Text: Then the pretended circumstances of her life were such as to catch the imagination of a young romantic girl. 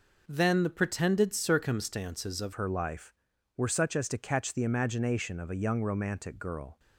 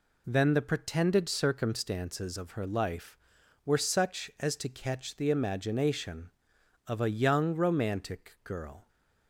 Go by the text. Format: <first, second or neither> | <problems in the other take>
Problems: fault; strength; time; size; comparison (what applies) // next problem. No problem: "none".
second | changes voice at "her"; from 2.5 s on; 4.2 s long